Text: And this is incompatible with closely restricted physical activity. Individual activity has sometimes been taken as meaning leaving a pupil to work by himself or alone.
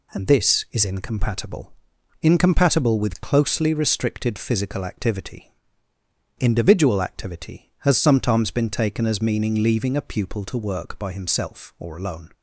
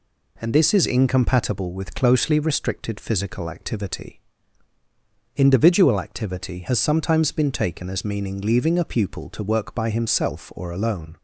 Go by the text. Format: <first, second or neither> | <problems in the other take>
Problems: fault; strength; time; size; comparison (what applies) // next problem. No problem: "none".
second | says "incompatible" twice; at 2.2 s